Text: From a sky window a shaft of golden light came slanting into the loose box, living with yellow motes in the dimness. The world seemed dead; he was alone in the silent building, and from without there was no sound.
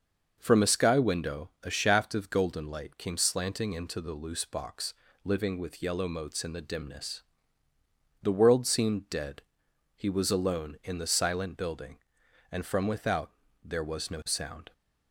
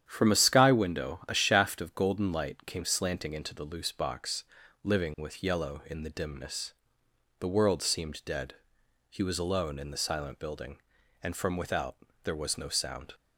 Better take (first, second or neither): first